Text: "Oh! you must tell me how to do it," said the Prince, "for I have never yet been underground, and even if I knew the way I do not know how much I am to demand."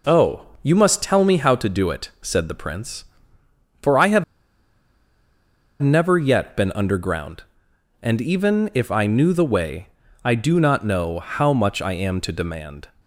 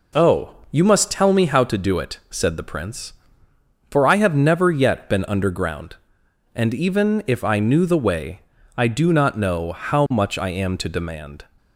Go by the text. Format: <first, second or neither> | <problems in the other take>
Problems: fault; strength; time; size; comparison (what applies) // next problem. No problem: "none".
second | pauses between "have" and "never"; strong; at 4.2 s; 1.5 s long // pauses between "way" and "I"; slight; at 9.8 s; 0.36 s long; slight in the second